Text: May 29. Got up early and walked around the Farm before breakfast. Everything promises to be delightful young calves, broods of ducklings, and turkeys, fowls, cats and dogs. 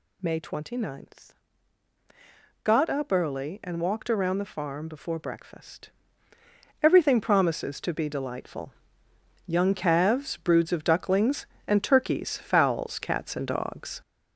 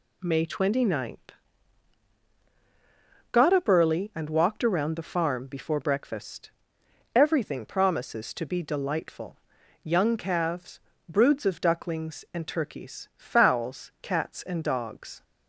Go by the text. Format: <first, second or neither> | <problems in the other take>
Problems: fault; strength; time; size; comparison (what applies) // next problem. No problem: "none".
second | gets louder; noticeable; throughout; 6 dB // pauses between "delightful" and "young"; noticeable; at 8.7 s; 0.76 s long; noticeable in the second